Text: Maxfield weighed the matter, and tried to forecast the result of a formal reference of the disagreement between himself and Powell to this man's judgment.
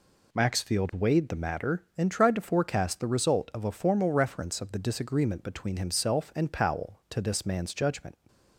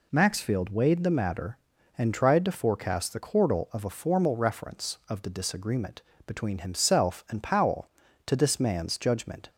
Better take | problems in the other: first | says "chordal" for "result"; at 3.1 s // pauses between "disagreement" and "between"; slight; at 6.0 s; 0.24 s long

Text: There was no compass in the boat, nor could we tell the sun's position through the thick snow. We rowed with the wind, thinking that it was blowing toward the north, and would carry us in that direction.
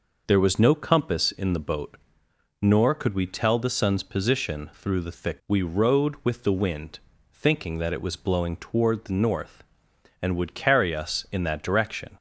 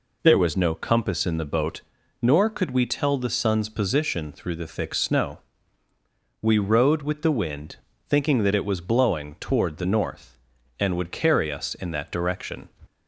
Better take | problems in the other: second | skips "snow"; at 5.4 s

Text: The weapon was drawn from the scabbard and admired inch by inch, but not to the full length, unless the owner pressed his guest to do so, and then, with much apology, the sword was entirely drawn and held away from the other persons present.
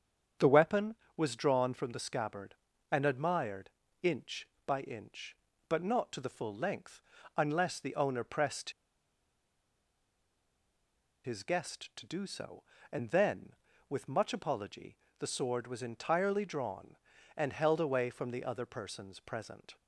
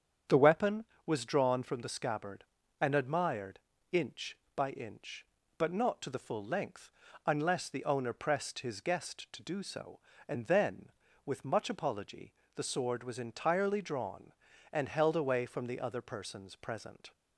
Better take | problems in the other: second | starts louder than the rest; strong; until 1.6 s; 8 dB; strong in the second // pauses between "admired" and "inch"; slight; at 3.6 s; 0.32 s long; slight in the second // pauses between "pressed" and "his"; strong; at 8.6 s; 2.5 s long

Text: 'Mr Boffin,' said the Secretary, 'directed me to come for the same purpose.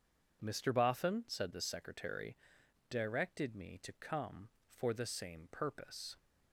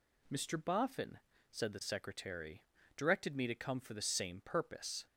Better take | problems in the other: neither | none

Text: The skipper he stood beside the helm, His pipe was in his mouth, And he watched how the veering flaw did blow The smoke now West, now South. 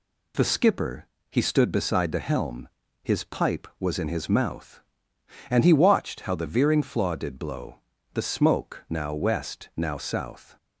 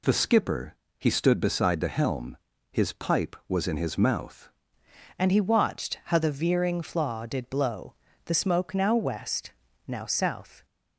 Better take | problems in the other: first | pauses between "skipper" and "he"; slight; at 0.7 s; 0.24 s long; slight in the first // changes voice at "And"; from 5.1 s on; 5.5 s long // pauses between "blow" and "The"; slight; at 7.9 s; 0.32 s long; slight in the first

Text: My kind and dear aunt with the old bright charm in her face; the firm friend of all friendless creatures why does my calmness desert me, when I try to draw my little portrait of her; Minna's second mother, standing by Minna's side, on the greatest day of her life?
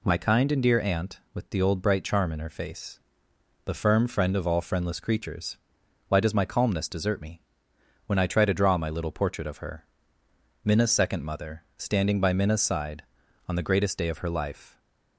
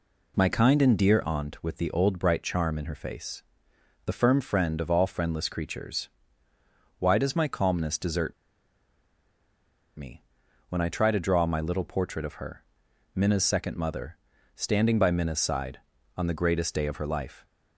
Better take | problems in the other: first | pauses between "creatures" and "why"; noticeable; at 6.0 s; 0.90 s long; noticeable in the first // pauses between "desert" and "me"; strong; at 8.3 s; 1.6 s long

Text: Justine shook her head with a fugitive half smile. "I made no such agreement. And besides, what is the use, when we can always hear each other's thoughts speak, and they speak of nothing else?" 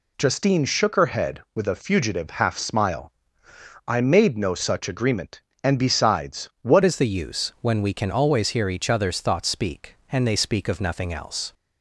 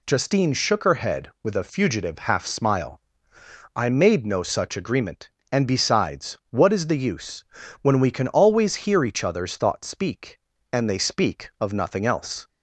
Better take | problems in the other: second | changes voice at "is"; from 6.8 s on; 4.7 s long

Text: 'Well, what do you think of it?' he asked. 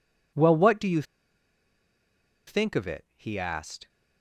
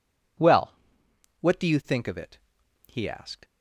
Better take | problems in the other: second | pauses between "you" and "think"; strong; at 1.0 s; 1.4 s long

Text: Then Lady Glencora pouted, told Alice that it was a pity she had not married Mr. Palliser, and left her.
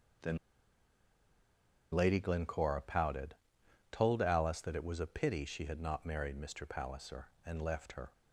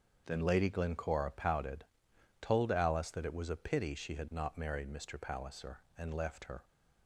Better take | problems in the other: second | starts louder than the rest; strong; until 2.7 s; 7 dB; also in the second // pauses between "Then" and "Lady"; strong; at 0.3 s; 1.5 s long

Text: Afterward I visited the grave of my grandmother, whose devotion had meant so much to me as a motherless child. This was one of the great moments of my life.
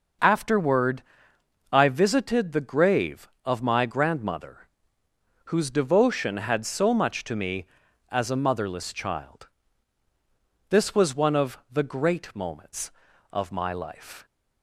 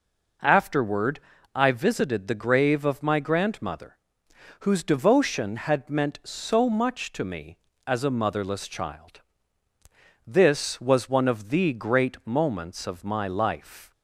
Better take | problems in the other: second | starts louder than the rest; noticeable; until 1.9 s; 6 dB // pauses between "Afterward" and "I"; noticeable; at 1.0 s; 0.70 s long; slight in the second // skips "meant"; at 6.6 s

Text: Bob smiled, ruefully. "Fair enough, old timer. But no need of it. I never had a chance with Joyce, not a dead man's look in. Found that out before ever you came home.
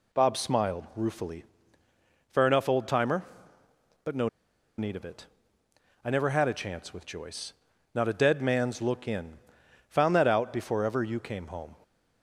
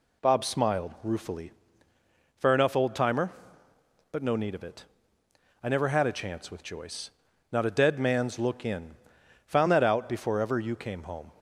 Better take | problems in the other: second | pauses between "no" and "need"; noticeable; at 4.2 s; 0.50 s long

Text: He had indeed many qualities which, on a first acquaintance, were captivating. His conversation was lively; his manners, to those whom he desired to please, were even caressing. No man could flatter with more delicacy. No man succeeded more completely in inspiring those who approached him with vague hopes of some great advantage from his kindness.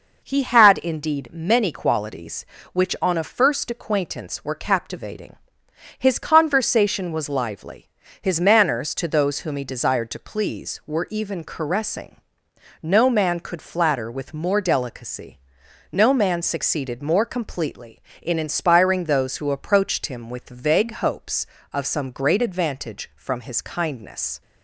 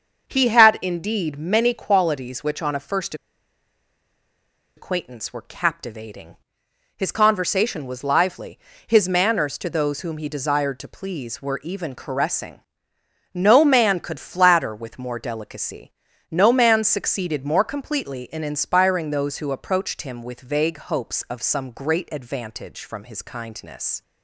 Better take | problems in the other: first | starts louder than the rest; until 1.3 s; 6 dB // pauses between "first" and "acquaintance"; strong; at 3.1 s; 1.6 s long

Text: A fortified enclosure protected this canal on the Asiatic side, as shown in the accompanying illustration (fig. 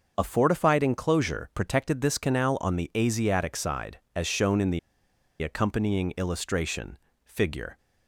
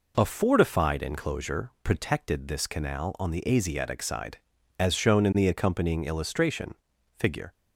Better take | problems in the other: second | starts louder than the rest; until 1.1 s; 6.5 dB // pauses between "the" and "accompanying"; noticeable; at 4.7 s; 0.61 s long

